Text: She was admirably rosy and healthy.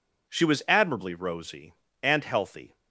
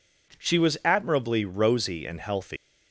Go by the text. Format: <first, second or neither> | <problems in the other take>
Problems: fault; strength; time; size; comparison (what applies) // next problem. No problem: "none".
first | leaves "healthy" unfinished; at 2.5 s; 160 ms